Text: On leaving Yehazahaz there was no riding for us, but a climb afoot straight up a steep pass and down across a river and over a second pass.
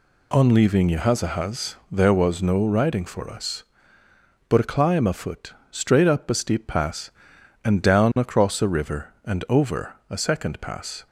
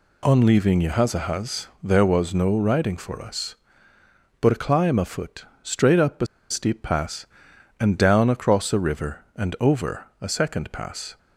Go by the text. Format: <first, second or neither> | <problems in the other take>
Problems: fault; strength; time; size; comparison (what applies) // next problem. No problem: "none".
first | pauses between "afoot" and "straight"; slight; at 5.4 s; 0.18 s long; slight in the first // pauses between "a" and "steep"; slight; at 6.2 s; 0.24 s long // pauses between "over" and "a"; slight; at 10.0 s; 0.16 s long; slight in the first